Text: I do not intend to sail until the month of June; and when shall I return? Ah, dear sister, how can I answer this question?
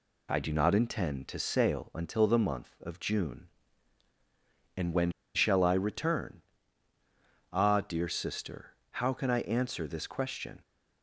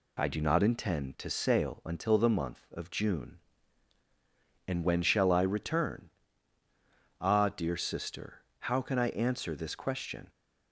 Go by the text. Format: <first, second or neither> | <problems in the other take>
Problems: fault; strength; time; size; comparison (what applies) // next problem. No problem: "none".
second | pauses between "when" and "shall"; slight; at 5.0 s; 0.25 s long